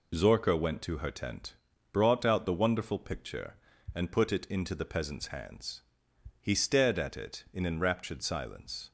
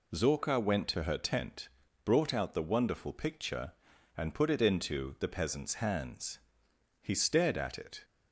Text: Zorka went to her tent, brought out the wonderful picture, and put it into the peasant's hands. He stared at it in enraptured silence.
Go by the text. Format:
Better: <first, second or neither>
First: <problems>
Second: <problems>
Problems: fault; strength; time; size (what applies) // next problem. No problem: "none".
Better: first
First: none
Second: stops before "in enraptured silence"; at 8.0 s